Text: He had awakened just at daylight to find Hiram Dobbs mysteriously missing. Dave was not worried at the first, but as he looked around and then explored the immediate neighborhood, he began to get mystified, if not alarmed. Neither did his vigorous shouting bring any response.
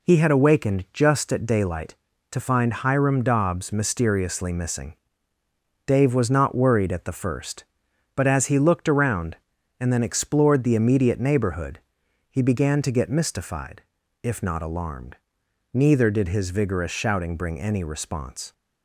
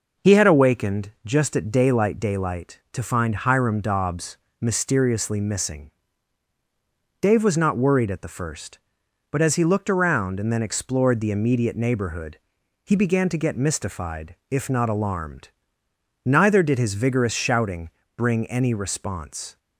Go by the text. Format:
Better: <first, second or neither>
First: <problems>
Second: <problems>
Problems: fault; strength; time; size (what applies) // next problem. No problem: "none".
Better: first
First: none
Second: says "daylight" twice; at 2.1 s // pauses between "Dobbs" and "mysteriously"; slight; at 4.3 s; 0.24 s long // pauses between "shouting" and "bring"; slight; at 17.8 s; 0.26 s long